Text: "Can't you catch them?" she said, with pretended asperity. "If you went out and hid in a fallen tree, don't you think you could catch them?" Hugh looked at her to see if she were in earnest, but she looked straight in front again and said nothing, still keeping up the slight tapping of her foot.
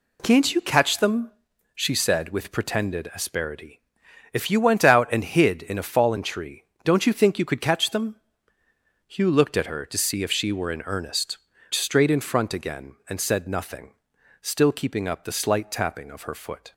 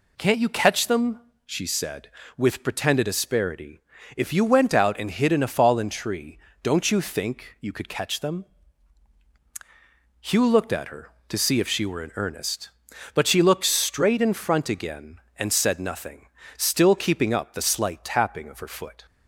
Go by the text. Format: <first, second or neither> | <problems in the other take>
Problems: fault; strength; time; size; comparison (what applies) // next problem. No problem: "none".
second | skips "but she looked"; at 11.5 s